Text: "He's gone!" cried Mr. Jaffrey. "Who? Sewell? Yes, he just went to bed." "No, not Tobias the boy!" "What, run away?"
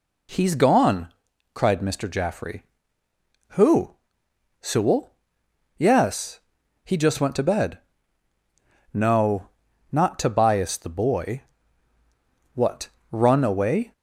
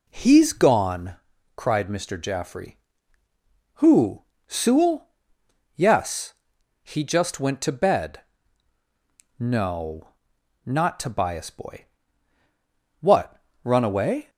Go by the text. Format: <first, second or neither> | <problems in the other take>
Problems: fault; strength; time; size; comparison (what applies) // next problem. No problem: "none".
first | skips "the"; at 11.4 s